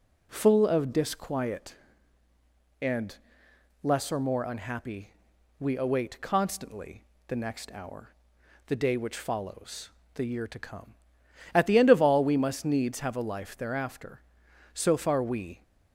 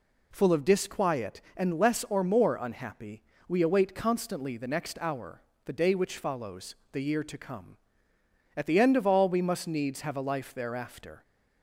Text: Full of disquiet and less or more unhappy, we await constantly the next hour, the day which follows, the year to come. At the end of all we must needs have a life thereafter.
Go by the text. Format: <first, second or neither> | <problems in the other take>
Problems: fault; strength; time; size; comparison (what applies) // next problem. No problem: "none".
second | pauses between "and" and "less"; noticeable; at 3.1 s; 0.66 s long // pauses between "constantly" and "the"; slight; at 7.0 s; 0.24 s long // goes on to say "So far we"; noticeable; from 14.7 s on; 0.90 s long